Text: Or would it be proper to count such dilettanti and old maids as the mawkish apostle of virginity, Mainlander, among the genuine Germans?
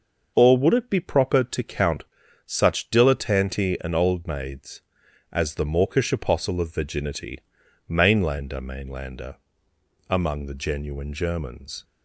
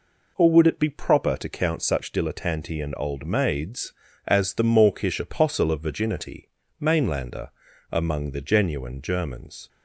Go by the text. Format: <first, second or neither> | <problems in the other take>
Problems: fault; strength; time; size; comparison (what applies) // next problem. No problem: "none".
second | pauses between "count" and "such"; at 2.0 s; 0.42 s long // says "Mainlander" twice; at 8.5 s